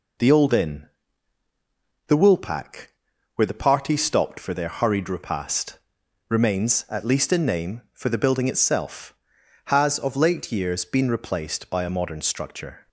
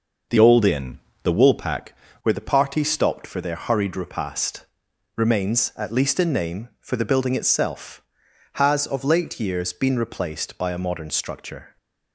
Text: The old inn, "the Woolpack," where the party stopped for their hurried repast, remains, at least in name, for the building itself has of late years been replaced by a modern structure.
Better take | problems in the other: first | changes voice from "old" to "Woolpack"; from 0.3 to 1.9 s; 1.6 s long

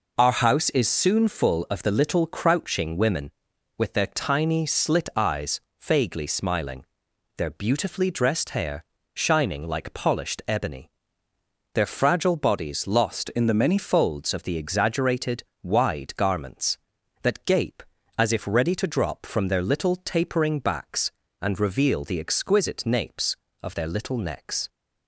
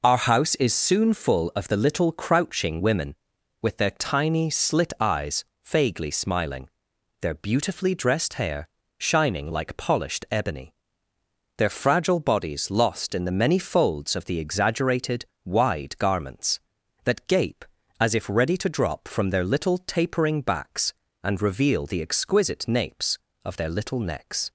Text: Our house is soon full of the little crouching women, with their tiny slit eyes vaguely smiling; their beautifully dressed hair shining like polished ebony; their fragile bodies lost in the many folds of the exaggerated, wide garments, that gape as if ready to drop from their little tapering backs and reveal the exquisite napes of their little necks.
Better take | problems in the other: second | pauses between "eyes" and "vaguely"; slight; at 5.5 s; 0.22 s long; slight in the second // pauses between "hair" and "shining"; slight; at 8.8 s; 0.30 s long; slight in the second // changes voice from "in" to "many"; from 13.2 to 13.7 s; 0.5 s long

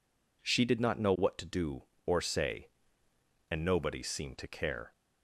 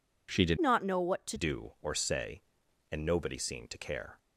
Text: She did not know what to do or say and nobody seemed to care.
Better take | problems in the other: first | changes voice from "not" to "to"; from 0.5 to 1.3 s; 0.8 s long

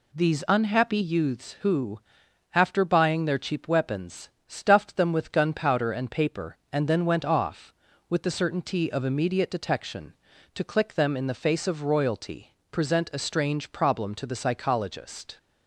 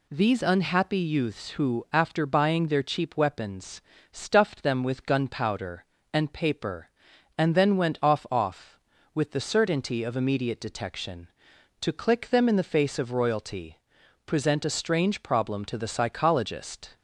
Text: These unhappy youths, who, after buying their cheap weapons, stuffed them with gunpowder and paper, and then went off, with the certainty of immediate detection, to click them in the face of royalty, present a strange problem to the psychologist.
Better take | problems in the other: first | says "off" twice; at 8.3 s

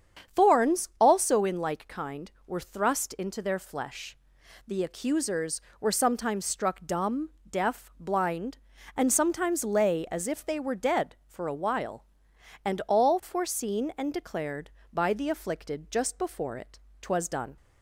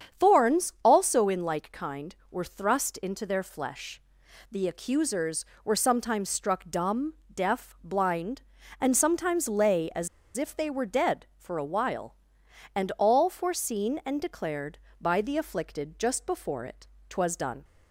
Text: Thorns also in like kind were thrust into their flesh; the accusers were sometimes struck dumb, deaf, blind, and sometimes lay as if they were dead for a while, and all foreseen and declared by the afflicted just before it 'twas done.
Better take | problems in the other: first | starts louder than the rest; strong; until 1.3 s; 7.5 dB; strong in the first // pauses between "as" and "if"; slight; at 10.0 s; 0.27 s long // pauses between "it" and "twas"; slight; at 16.8 s; 0.20 s long; slight in the first

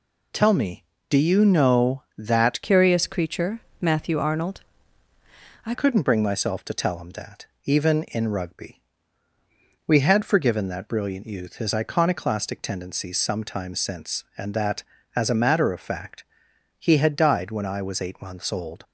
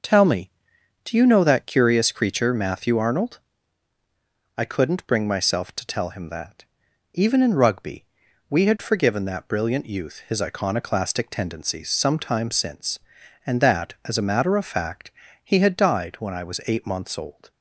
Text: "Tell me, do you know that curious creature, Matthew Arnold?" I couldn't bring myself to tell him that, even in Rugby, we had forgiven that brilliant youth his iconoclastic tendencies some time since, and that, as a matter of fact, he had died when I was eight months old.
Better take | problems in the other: second | changes voice from "curious" to "I"; from 2.6 to 5.7 s; 3.1 s long

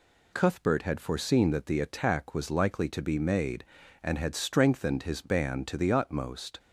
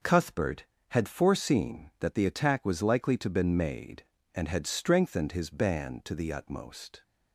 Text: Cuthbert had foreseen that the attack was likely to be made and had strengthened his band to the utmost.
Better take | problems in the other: first | says "been" for "be"; at 3.2 s

